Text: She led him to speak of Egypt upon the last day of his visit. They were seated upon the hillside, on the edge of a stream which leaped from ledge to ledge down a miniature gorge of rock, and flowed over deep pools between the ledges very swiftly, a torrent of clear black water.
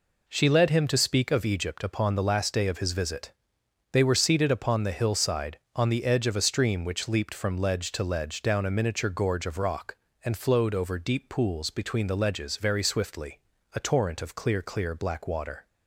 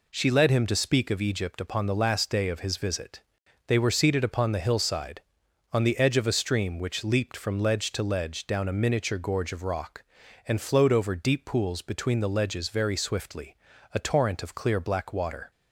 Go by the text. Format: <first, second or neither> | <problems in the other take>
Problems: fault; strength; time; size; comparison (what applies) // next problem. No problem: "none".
second | says "clear" twice; at 14.6 s